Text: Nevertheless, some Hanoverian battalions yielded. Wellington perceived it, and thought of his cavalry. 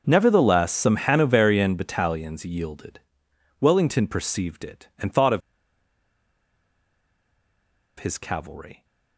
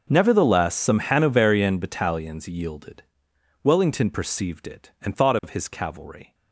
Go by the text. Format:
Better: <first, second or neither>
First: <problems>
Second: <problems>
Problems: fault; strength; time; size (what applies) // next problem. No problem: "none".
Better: second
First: pauses between "of" and "his"; strong; at 5.4 s; 2.5 s long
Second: none